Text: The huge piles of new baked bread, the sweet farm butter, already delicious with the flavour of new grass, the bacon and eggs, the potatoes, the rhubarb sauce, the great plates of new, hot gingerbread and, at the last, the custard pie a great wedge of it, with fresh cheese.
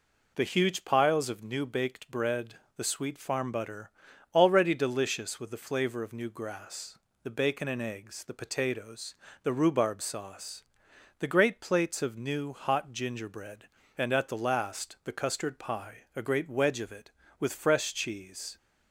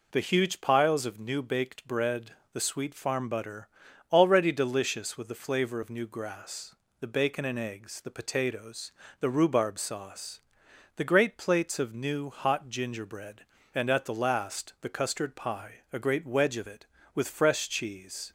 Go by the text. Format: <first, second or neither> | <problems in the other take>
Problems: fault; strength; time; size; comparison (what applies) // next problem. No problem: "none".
neither | none